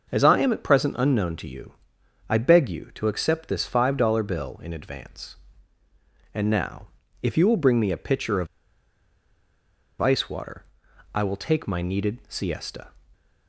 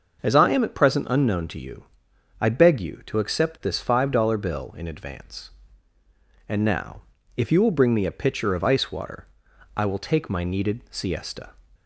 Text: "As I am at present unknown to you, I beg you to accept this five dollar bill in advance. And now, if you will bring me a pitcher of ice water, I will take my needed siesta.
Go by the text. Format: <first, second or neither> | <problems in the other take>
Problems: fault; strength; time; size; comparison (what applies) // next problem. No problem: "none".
second | starts louder than the rest; noticeable; until 1.1 s; 6 dB; noticeable in the second // pauses between "of" and "ice"; strong; at 8.4 s; 1.5 s long